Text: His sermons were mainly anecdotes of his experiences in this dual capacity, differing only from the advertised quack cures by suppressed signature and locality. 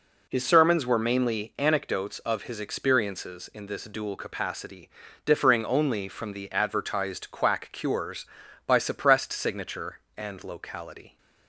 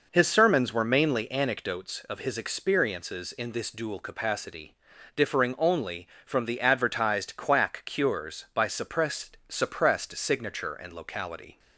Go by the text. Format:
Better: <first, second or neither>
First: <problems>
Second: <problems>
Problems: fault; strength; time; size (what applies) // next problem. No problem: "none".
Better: first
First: none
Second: says "suppressed" twice; at 9.4 s